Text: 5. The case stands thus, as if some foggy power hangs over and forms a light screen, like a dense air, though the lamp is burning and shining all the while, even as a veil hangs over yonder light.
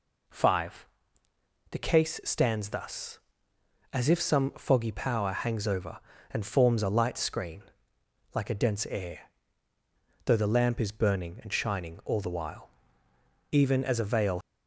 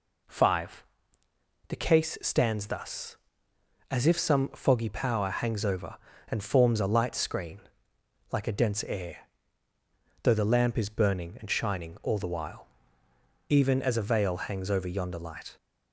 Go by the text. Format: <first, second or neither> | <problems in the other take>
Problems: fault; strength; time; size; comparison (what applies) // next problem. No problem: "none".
second | stops before "hangs over yonder light"; at 14.4 s